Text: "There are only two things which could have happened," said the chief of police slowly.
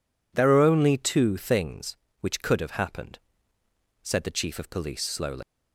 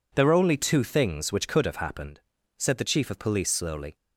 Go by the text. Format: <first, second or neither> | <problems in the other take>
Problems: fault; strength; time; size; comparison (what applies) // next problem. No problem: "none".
second | leaves "slowly" unfinished; at 5.4 s; 135 ms